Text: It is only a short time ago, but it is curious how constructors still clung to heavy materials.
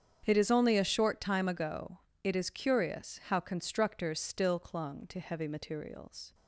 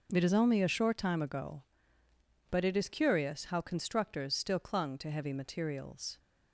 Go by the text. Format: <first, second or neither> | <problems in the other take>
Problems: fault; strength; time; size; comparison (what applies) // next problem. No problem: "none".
second | starts louder than the rest; strong; until 1.2 s; 7.5 dB; noticeable in the second // skips "but"; at 2.1 s